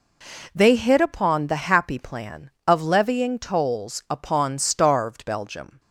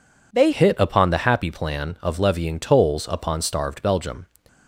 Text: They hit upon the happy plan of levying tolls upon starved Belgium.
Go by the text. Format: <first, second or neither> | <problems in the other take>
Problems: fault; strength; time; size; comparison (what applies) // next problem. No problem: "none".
first | changes voice at "hit"; from 0.5 s on; 3.7 s long